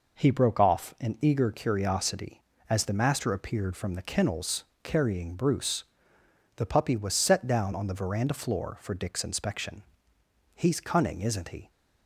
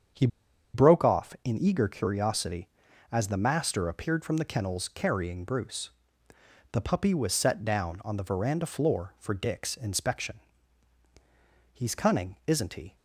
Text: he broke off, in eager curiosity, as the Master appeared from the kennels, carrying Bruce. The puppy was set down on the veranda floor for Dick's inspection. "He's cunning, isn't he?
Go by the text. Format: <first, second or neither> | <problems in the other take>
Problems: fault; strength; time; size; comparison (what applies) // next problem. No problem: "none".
first | starts louder than the rest; strong; until 1.7 s; 7.5 dB // pauses between "he" and "broke"; noticeable; at 0.2 s; 0.46 s long